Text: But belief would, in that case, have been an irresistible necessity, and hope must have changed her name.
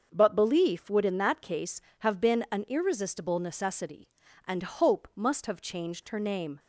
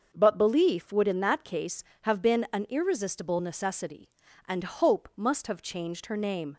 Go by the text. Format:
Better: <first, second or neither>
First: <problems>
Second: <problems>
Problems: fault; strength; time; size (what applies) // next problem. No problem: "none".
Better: neither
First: starts louder than the rest; until 1.1 s; 6.5 dB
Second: starts louder than the rest; until 1.1 s; 6.5 dB